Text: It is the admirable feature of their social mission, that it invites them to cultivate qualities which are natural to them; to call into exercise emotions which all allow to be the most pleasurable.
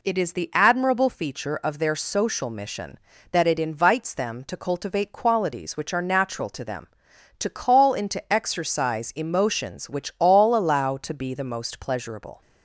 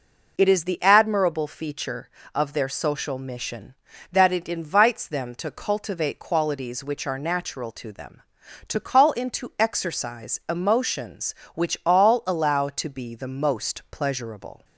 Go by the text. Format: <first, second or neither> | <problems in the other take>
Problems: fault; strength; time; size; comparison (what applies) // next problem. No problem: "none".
neither | none